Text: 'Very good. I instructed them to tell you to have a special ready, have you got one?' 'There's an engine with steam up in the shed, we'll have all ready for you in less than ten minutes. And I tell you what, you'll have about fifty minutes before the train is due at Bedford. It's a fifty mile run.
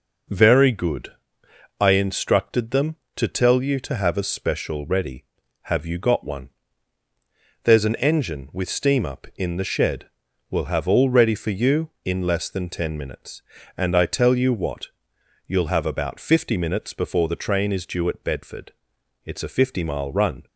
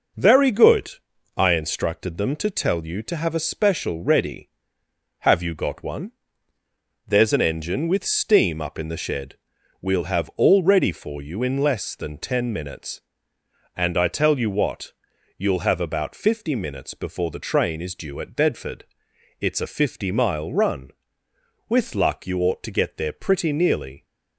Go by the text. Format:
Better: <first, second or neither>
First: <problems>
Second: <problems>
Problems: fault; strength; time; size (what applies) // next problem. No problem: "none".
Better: first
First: none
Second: goes on to say "With luck you ought to get there pretty nearly"; strong; from 21.6 s on; 2.3 s long